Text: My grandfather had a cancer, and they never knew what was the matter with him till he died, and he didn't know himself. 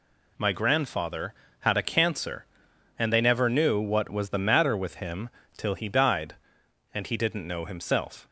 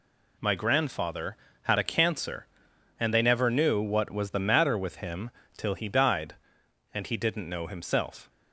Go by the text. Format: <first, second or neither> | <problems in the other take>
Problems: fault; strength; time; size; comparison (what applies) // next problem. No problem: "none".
neither | pauses between "him" and "till"; slight; the same in both